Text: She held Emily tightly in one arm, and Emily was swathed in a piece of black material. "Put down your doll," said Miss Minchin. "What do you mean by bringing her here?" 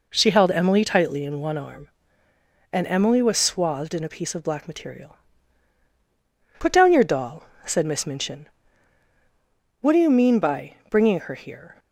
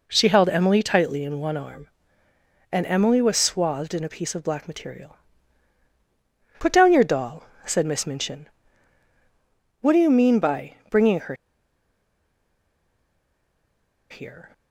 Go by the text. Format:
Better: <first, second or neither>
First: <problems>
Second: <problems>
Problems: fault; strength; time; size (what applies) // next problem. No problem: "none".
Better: first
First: pauses between "by" and "bringing"; slight; at 10.7 s; 0.16 s long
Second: pauses between "by" and "bringing"; slight; at 10.7 s; 0.16 s long // pauses between "her" and "here"; strong; at 11.3 s; 2.7 s long